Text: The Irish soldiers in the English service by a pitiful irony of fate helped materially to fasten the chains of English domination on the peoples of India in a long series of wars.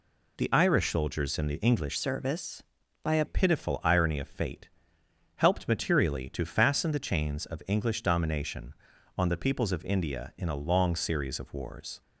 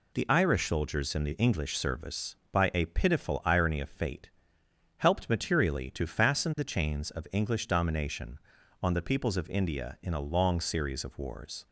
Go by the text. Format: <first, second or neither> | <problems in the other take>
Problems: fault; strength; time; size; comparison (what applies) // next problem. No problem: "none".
second | changes voice from "service" to "a"; from 1.9 to 3.2 s; 1.3 s long // pauses between "fate" and "helped"; noticeable; at 4.6 s; 0.70 s long; noticeable in the second